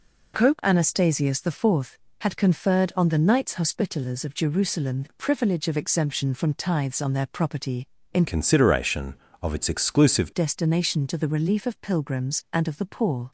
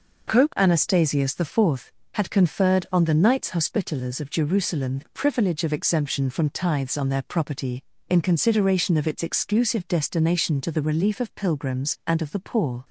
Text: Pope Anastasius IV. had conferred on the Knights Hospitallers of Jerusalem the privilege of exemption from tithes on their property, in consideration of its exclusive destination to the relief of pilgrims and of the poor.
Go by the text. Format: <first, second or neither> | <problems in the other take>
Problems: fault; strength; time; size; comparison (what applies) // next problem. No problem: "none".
second | changes voice from "consideration" to "exclusive"; from 8.2 to 10.3 s; 2.1 s long